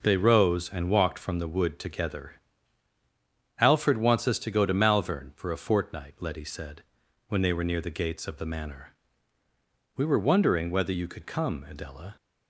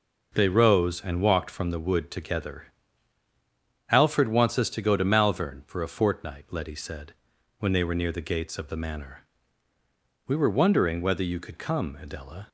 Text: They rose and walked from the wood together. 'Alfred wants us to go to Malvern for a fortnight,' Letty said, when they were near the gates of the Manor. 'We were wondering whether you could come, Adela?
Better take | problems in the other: neither | none

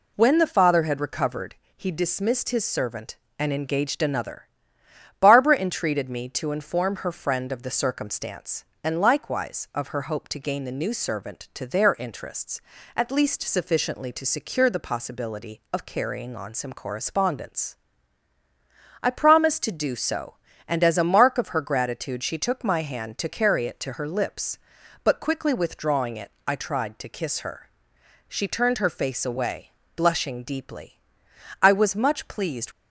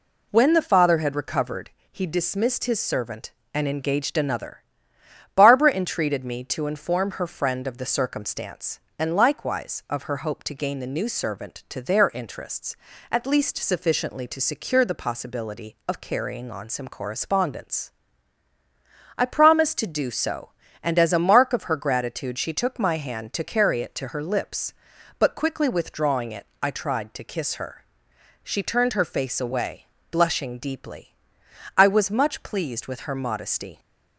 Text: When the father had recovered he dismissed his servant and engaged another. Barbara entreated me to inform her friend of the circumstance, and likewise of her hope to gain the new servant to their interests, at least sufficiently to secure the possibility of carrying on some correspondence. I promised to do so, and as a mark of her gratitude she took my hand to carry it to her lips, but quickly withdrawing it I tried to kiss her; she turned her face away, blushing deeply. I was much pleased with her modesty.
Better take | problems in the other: second | pauses between "recovered" and "he"; slight; at 1.5 s; 0.20 s long; slight in the second // pauses between "it" and "I"; slight; at 26.2 s; 0.16 s long; slight in the second // stops before "with her modesty"; at 32.7 s

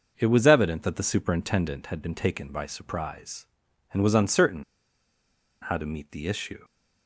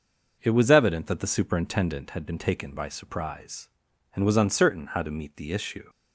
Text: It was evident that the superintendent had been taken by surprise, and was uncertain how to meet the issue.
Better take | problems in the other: second | pauses between "uncertain" and "how"; at 4.6 s; 1.0 s long

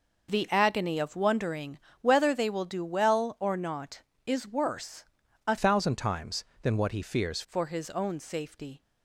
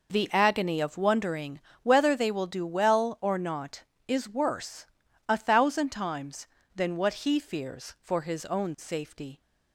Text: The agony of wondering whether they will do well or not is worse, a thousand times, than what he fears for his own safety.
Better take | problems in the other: second | pauses between "wondering" and "whether"; slight; at 1.7 s; 0.22 s long; slight in the second // changes voice from "thousand" to "fears"; from 5.5 to 7.4 s; 1.9 s long

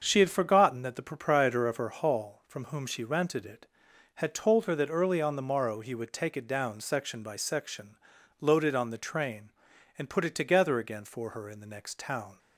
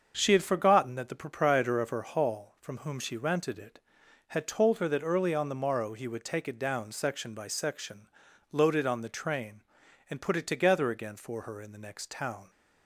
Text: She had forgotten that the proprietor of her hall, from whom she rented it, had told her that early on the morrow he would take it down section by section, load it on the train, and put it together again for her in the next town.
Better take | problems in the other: neither | starts louder than the rest; the same in both

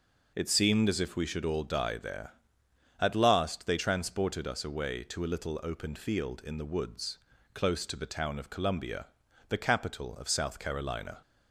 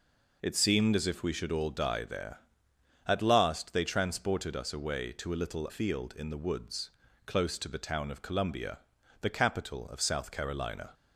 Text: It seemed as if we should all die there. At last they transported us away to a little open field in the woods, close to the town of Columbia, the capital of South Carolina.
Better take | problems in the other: first | skips "open"; at 5.6 s

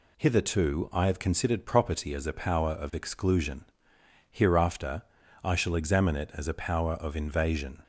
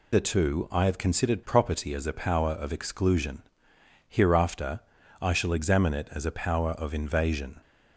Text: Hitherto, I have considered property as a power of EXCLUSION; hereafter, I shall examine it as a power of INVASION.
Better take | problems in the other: first | loses the start of "Hitherto"; at 0.1 s; 170 ms

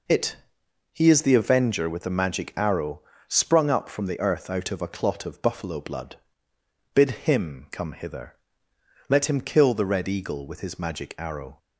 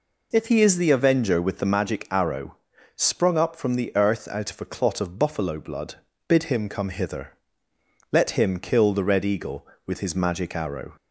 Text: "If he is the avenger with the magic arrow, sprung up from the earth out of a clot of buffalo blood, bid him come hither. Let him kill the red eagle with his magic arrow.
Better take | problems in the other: second | says "It" for "If"; at 0.0 s

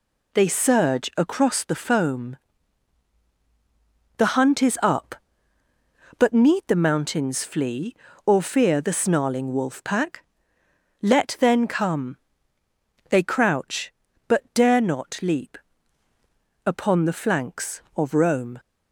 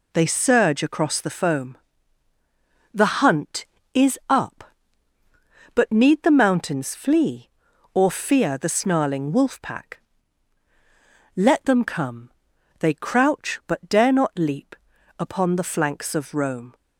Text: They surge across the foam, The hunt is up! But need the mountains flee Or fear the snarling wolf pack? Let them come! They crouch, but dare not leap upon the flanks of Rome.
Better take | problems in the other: second | says "then" for "them"; at 11.3 s // pauses between "leap" and "upon"; at 15.5 s; 1.0 s long; also in the second

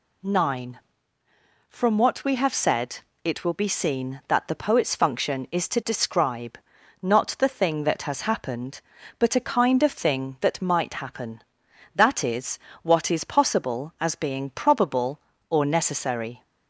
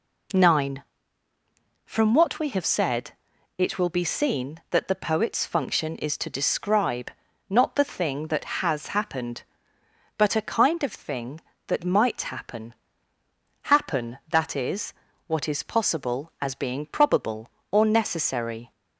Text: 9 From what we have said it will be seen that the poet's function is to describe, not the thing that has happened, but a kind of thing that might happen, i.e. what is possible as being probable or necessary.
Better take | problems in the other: first | pauses between "said" and "it"; noticeable; at 3.1 s; 0.46 s long; slight in the first // says "happen" twice; at 13.6 s

